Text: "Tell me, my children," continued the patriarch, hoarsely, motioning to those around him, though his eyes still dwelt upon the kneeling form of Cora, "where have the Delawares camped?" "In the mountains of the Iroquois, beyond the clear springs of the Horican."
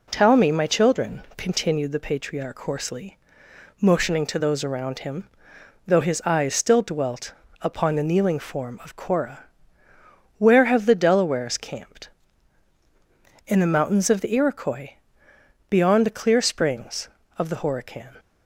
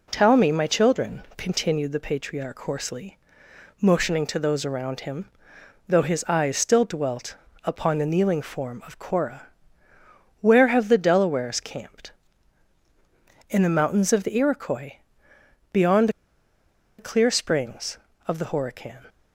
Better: first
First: pauses between "dwelt" and "upon"; slight; at 7.3 s; 0.28 s long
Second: pauses between "dwelt" and "upon"; slight; at 7.3 s; 0.28 s long // pauses between "beyond" and "the"; noticeable; at 16.0 s; 0.89 s long

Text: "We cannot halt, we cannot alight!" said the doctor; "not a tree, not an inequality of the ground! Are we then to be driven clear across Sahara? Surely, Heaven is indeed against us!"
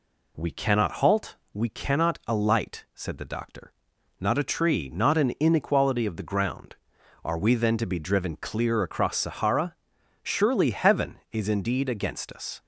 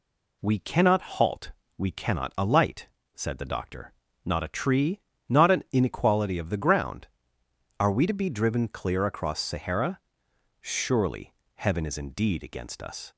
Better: first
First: none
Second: skips "then"; at 8.0 s

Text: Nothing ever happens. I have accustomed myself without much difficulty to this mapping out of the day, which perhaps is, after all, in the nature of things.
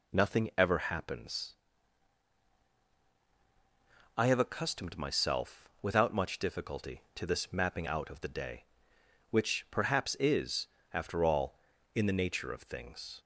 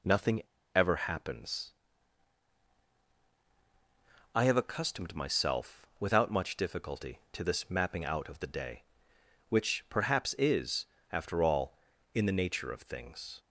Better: first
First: none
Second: pauses between "Nothing" and "ever"; slight; at 0.4 s; 0.33 s long

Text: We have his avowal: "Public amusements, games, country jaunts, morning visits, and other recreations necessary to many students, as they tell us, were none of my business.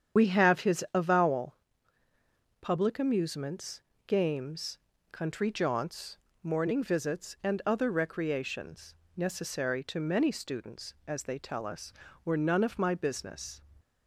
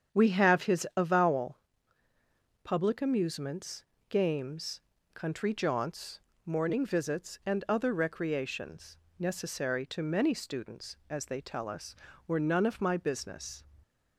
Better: second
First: loses the start of "We"; at 0.1 s; 65 ms // starts louder than the rest; strong; until 1.2 s; 8.5 dB // pauses between "recreations" and "necessary"; slight; at 8.9 s; 0.22 s long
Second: starts louder than the rest; strong; until 1.2 s; 8 dB // pauses between "recreations" and "necessary"; slight; at 8.9 s; 0.22 s long

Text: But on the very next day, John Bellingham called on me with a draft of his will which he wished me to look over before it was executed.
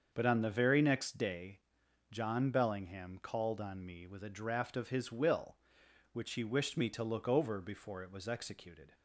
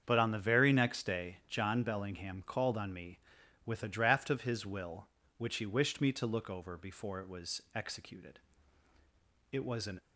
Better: first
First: starts louder than the rest; until 1.1 s; 6.5 dB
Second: starts louder than the rest; strong; until 1.0 s; 7.5 dB // goes on to say "It was an"; slight; from 9.5 s on; 0.48 s long

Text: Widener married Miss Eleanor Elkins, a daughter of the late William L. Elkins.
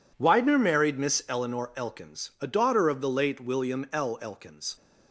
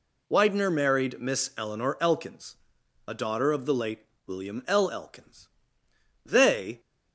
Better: first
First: none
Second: pauses between "late" and "William"; slight; at 3.9 s; 0.26 s long // goes on to say "They"; from 6.2 s on; 0.56 s long

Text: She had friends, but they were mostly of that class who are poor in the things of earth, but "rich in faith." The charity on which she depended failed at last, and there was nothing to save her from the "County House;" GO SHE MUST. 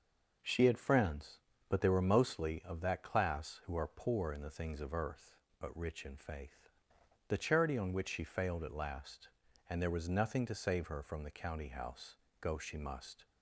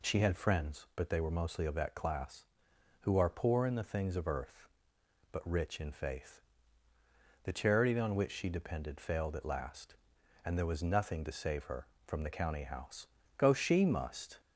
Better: second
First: skips "depended"; at 8.2 s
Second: none

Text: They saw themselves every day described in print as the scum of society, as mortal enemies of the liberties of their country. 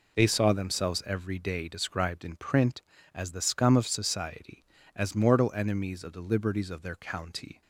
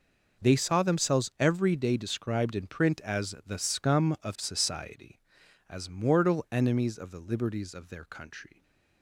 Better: second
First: says "county" for "country"; at 6.9 s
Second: none

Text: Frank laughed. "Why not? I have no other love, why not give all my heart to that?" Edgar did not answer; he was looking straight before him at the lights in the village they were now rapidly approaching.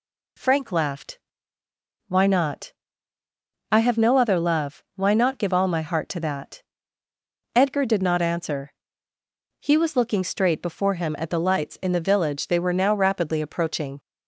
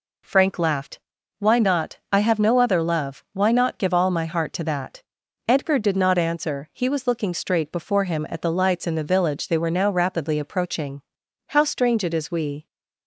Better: first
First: none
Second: goes on to say "How strange it is we"; noticeable; from 11.4 s on; 1.1 s long

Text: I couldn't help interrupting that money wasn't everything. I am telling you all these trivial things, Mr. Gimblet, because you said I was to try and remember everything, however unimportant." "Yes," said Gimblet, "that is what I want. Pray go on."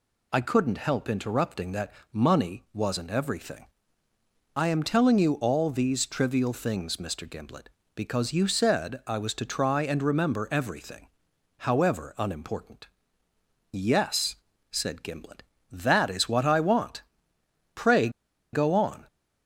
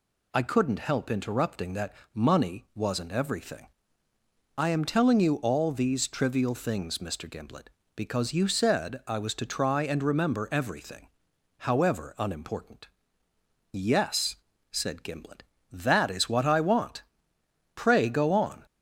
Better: second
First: pauses between "that" and "money"; slight; at 1.9 s; 0.18 s long // pauses between "Pray" and "go"; at 18.0 s; 0.43 s long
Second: pauses between "that" and "money"; slight; at 1.9 s; 0.18 s long

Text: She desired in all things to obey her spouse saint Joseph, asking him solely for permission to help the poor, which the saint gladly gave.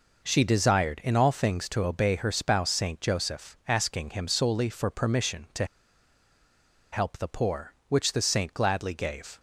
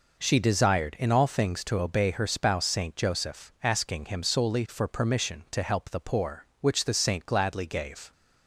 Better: second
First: pauses between "to" and "help"; strong; at 5.6 s; 1.2 s long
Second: none

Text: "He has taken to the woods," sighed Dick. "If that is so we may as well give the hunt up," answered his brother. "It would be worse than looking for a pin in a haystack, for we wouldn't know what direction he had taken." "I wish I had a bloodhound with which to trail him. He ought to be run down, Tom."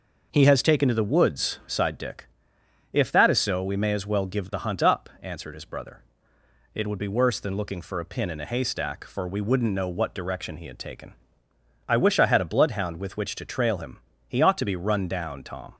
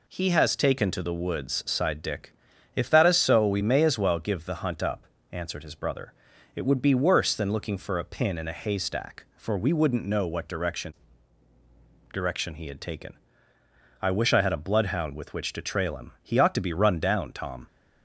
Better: first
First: none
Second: says "direction" twice; at 12.1 s

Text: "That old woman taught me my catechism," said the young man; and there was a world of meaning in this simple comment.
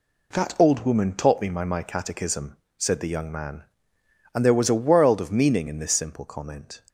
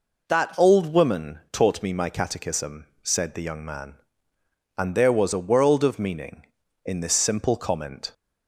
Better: second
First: says "my" twice; at 1.6 s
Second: none

